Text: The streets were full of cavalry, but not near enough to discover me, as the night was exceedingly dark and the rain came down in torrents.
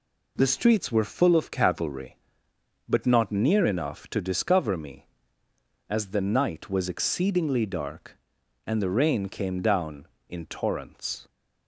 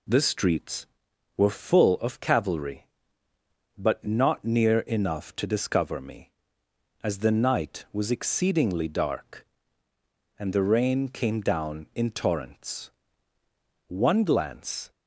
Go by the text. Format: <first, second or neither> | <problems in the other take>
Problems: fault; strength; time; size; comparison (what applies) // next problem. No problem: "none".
first | goes on to say "One glance"; noticeable; from 13.8 s on; 1.0 s long